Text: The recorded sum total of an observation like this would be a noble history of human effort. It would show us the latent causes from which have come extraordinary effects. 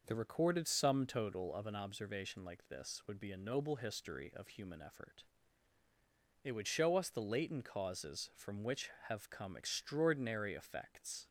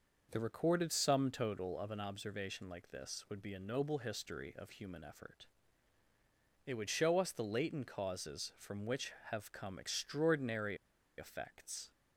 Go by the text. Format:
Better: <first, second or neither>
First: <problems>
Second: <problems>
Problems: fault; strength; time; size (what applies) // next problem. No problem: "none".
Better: first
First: none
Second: pauses between "extraordinary" and "effects"; at 10.7 s; 0.42 s long